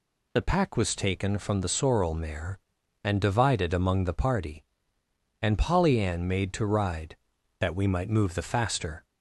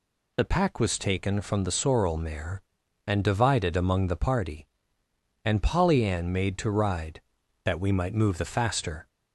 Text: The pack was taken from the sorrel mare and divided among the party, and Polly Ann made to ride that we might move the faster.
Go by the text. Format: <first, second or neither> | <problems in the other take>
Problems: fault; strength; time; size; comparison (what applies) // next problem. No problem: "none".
neither | none